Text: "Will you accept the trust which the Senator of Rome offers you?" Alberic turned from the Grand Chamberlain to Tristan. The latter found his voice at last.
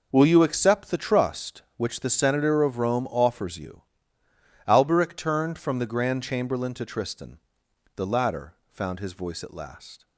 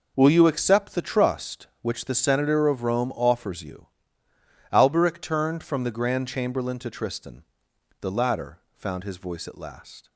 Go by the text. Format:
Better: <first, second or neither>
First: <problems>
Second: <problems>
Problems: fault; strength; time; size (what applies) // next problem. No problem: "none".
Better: neither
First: pauses between "latter" and "found"; slight; at 8.5 s; 0.18 s long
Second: pauses between "latter" and "found"; slight; at 8.5 s; 0.18 s long